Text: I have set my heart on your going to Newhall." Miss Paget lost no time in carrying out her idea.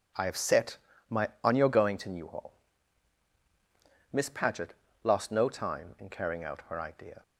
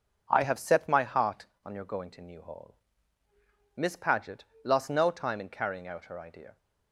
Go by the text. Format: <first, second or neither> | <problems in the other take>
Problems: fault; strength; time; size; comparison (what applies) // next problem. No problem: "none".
second | pauses between "set" and "my"; slight; at 0.7 s; 0.32 s long // skips "heart"; at 1.3 s // pauses between "Paget" and "lost"; slight; at 4.7 s; 0.32 s long; slight in the second